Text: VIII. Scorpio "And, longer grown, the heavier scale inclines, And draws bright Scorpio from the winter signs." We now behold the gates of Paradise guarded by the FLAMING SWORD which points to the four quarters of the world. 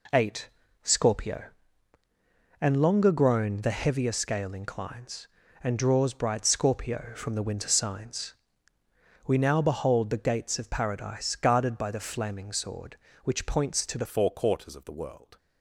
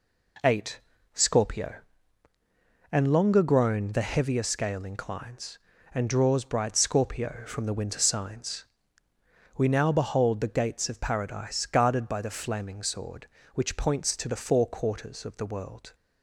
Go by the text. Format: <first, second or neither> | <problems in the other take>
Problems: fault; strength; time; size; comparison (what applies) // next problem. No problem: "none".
second | changes voice at "four"; from 14.0 s on; 1.3 s long